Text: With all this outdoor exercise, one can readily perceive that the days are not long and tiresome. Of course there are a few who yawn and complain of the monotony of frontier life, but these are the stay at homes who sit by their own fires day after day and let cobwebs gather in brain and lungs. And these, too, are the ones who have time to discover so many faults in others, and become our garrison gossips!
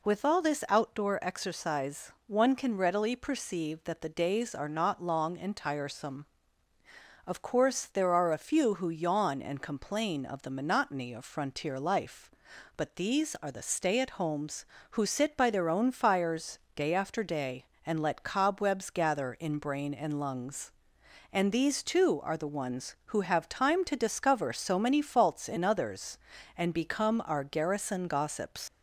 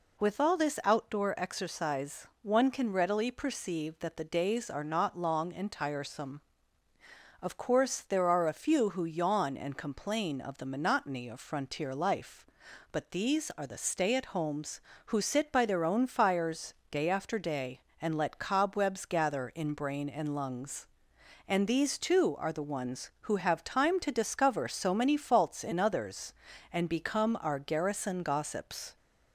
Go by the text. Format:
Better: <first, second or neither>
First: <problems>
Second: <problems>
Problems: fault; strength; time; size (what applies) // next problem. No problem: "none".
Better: second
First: pauses between "fires" and "day"; slight; at 16.5 s; 0.16 s long // leaves "gossips" unfinished; at 28.6 s; 125 ms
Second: pauses between "fires" and "day"; slight; at 16.7 s; 0.16 s long